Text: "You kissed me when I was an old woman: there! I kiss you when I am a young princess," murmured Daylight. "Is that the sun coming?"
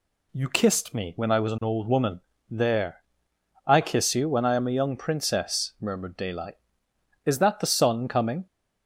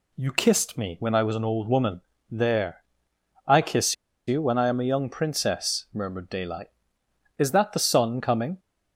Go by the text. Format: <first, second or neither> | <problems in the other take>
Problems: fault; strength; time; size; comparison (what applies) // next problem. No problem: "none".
first | pauses between "kiss" and "you"; slight; at 3.9 s; 0.32 s long